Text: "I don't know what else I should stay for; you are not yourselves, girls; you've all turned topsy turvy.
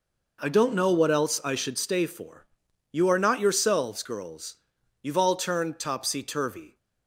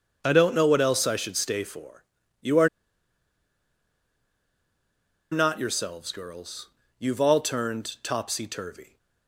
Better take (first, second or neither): first